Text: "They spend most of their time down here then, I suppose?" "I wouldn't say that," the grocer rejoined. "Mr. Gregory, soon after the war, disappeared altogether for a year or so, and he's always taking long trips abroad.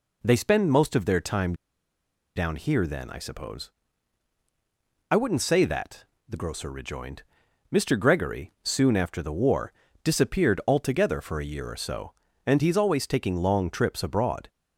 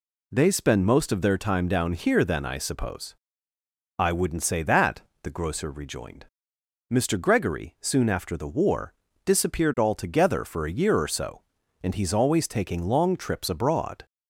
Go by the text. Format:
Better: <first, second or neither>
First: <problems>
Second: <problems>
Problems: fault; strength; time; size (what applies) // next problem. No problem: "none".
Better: second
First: pauses between "time" and "down"; noticeable; at 1.5 s; 0.80 s long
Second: none